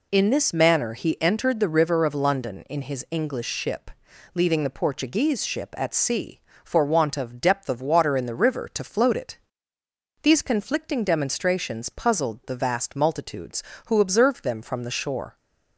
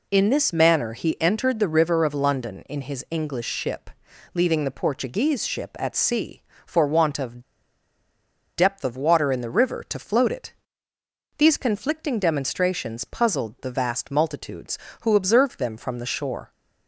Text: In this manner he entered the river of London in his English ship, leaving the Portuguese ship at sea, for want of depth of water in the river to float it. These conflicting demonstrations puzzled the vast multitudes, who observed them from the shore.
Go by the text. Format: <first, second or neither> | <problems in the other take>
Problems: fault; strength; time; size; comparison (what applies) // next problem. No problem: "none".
first | pauses between "of" and "depth"; at 7.4 s; 1.1 s long